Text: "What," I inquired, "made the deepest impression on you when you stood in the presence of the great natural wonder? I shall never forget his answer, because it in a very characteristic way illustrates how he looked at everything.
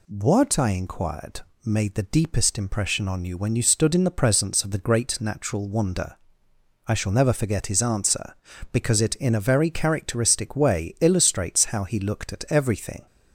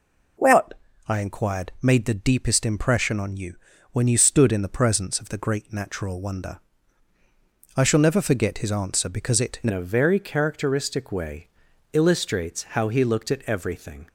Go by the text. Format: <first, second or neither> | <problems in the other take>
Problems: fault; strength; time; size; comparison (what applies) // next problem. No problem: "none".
first | pauses between "you" and "when"; slight; at 3.5 s; 0.34 s long // changes voice at "a"; from 9.6 s on; 4.4 s long // pauses between "way" and "illustrates"; at 11.4 s; 0.44 s long